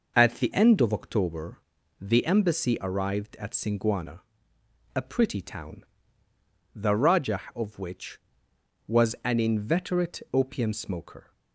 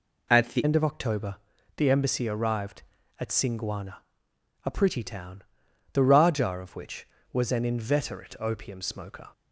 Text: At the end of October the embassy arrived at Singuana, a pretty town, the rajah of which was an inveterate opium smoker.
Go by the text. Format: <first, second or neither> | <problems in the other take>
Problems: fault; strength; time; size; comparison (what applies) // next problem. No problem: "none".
first | changes voice at "end"; from 0.6 s on; 8.6 s long // pauses between "October" and "the"; at 1.3 s; 0.40 s long; also in the first